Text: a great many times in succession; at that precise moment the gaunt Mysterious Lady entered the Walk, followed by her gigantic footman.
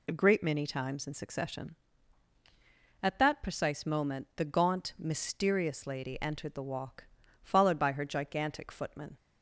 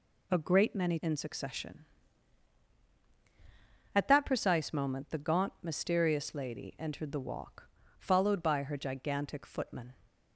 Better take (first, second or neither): first